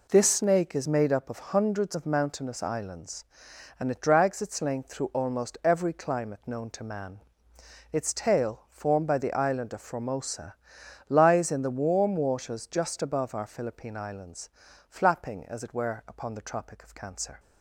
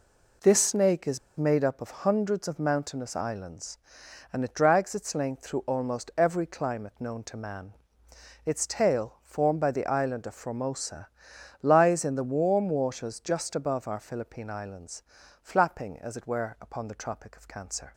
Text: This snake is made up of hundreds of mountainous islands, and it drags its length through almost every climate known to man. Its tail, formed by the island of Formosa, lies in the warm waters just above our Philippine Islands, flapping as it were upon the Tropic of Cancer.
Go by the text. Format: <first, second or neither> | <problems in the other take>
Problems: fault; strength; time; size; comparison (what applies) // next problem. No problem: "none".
first | pauses between "is" and "made"; slight; at 1.1 s; 0.18 s long